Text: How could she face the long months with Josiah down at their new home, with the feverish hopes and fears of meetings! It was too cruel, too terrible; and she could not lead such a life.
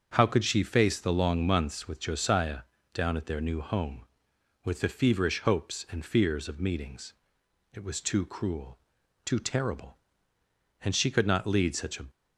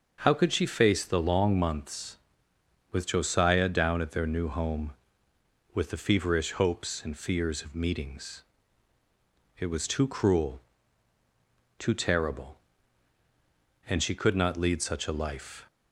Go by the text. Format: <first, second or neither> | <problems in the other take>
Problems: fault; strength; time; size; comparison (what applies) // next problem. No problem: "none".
second | starts louder than the rest; until 1.1 s; 6.5 dB; noticeable in the second // pauses between "Josiah" and "down"; slight; at 2.6 s; 0.28 s long // stops before "life"; at 12.0 s